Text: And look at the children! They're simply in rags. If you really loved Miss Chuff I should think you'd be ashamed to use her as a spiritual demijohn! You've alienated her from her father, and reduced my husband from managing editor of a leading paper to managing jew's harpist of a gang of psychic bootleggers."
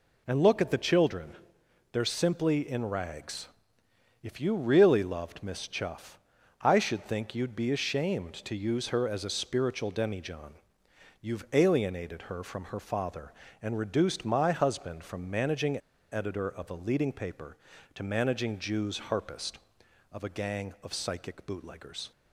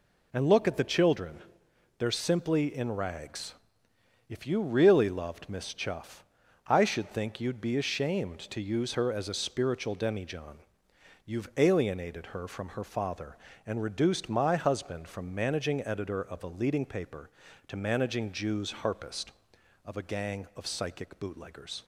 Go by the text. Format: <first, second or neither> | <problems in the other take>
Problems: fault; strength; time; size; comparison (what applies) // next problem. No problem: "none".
second | pauses between "Chuff" and "I"; at 6.1 s; 0.44 s long; also in the second // pauses between "managing" and "editor"; slight; at 15.7 s; 0.33 s long